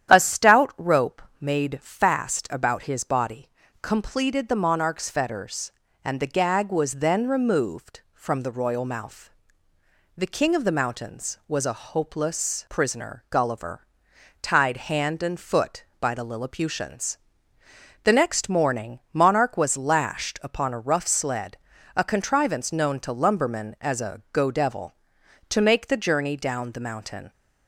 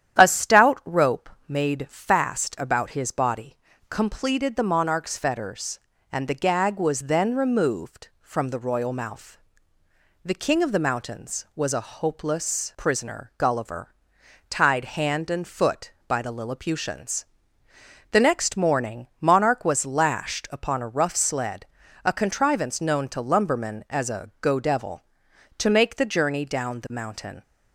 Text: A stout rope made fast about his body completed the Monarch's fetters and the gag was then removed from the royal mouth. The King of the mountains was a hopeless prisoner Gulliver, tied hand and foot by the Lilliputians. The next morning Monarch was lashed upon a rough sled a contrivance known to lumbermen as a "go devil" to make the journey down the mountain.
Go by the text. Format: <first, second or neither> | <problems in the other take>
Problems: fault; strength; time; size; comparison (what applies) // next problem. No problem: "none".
neither | starts louder than the rest; strong; the same in both // pauses between "rope" and "made"; slight; the same in both // pauses between "body" and "completed"; slight; the same in both // pauses between "sled" and "a"; slight; the same in both